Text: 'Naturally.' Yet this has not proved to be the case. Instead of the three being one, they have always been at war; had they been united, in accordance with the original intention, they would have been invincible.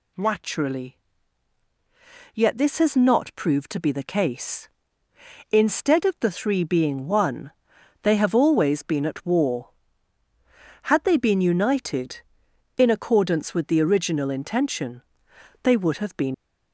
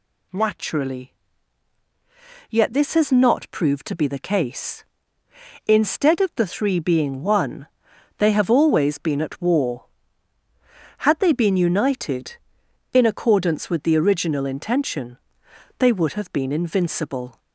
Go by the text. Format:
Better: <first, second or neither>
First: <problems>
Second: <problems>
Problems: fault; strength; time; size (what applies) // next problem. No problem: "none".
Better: second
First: stops before "invincible"; at 16.3 s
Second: none